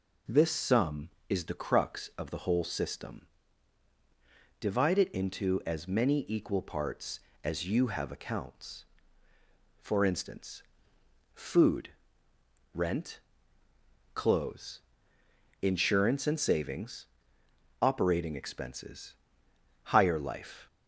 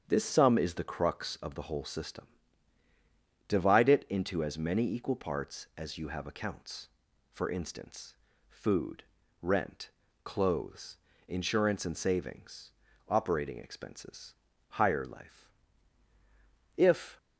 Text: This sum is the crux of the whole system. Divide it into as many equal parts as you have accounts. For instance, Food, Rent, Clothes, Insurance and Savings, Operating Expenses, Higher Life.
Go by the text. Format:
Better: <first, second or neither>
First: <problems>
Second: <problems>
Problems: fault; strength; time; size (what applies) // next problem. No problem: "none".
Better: first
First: none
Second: starts louder than the rest; strong; until 1.0 s; 8 dB // goes on to say "If"; slight; from 16.7 s on; 0.40 s long